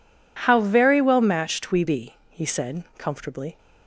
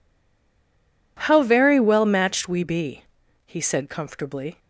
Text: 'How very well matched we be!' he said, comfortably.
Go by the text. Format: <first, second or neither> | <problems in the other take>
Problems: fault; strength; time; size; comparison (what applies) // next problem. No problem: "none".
first | stays silent before the first word; until 1.1 s; 1.1 s long